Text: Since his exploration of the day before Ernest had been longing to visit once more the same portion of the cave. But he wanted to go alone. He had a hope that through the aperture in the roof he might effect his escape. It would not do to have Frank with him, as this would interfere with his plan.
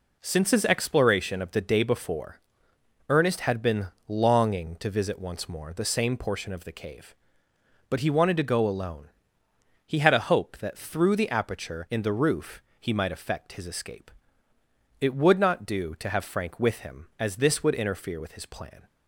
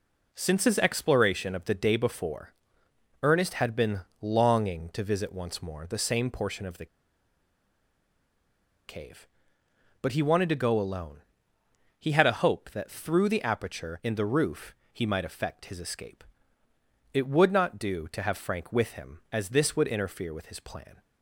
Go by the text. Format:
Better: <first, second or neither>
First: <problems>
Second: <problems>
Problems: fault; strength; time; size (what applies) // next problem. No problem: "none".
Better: first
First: pauses between "before" and "Ernest"; noticeable; at 2.4 s; 0.68 s long // pauses between "been" and "longing"; slight; at 3.8 s; 0.22 s long // pauses between "roof" and "he"; slight; at 12.6 s; 0.18 s long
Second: pauses between "before" and "Ernest"; noticeable; at 2.5 s; 0.68 s long // pauses between "been" and "longing"; slight; at 3.9 s; 0.22 s long // pauses between "the" and "cave"; strong; at 6.8 s; 2.0 s long // pauses between "roof" and "he"; slight; at 14.7 s; 0.18 s long